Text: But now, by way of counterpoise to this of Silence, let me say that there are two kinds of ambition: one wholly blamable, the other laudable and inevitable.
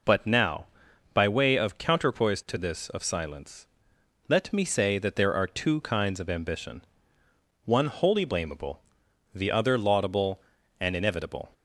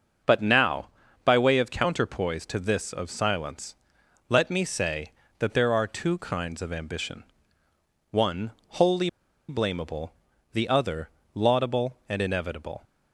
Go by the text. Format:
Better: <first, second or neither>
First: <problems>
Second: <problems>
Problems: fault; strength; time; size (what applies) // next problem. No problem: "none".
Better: first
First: none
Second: starts louder than the rest; until 1.6 s; 6.5 dB // pauses between "one" and "wholly"; slight; at 8.5 s; 0.16 s long // pauses between "wholly" and "blamable"; at 9.0 s; 0.40 s long // pauses between "other" and "laudable"; slight; at 11.0 s; 0.24 s long